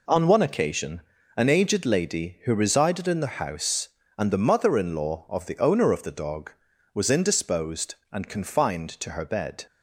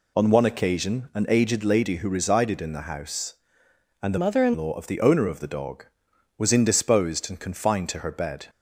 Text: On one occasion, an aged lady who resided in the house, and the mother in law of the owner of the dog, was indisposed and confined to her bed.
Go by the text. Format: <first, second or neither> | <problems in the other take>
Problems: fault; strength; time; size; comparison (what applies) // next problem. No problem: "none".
first | changes voice from "mother" to "in"; from 4.1 to 4.5 s; 0.4 s long